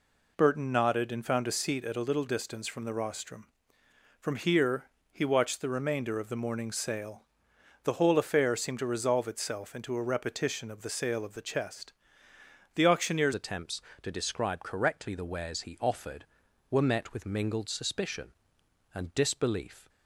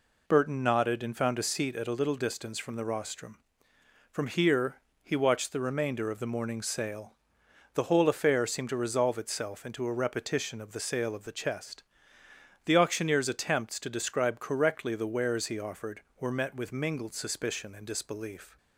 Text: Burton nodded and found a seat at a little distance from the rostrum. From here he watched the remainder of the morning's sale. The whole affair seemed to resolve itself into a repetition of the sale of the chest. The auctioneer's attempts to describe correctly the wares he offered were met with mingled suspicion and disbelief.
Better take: second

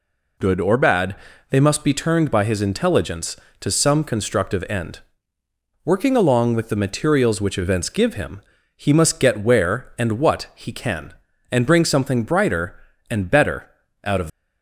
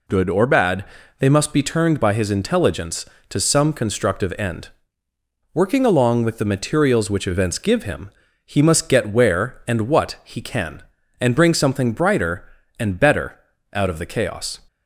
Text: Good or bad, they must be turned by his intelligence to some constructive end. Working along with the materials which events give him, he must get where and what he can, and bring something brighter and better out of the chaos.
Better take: second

